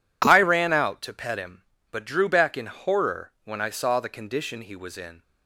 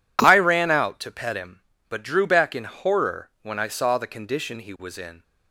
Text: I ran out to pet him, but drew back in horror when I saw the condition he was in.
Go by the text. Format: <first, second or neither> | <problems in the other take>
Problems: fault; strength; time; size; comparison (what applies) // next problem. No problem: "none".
neither | none